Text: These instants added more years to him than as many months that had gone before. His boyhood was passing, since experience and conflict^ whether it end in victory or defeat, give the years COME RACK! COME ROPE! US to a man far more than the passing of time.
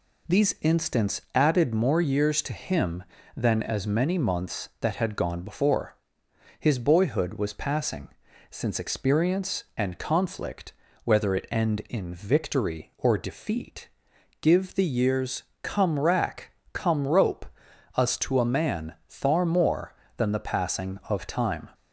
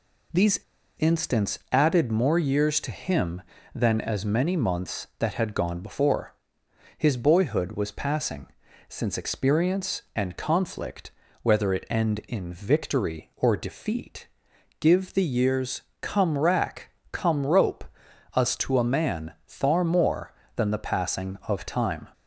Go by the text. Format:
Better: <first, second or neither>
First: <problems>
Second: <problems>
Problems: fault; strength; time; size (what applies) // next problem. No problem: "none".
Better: first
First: pauses between "conflict" and "whether"; slight; at 10.7 s; 0.30 s long // pauses between "years" and "COME"; slight; at 15.4 s; 0.18 s long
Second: pauses between "These" and "instants"; at 0.6 s; 0.38 s long // pauses between "conflict" and "whether"; slight; at 11.1 s; 0.30 s long // pauses between "years" and "COME"; slight; at 15.8 s; 0.18 s long